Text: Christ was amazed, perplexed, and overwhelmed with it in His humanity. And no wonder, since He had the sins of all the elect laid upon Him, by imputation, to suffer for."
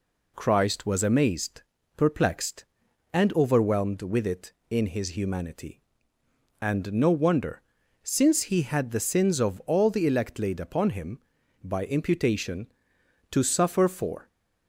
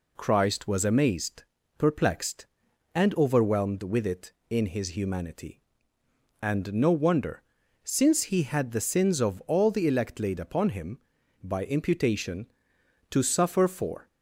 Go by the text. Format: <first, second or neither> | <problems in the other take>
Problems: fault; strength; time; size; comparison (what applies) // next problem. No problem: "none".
neither | none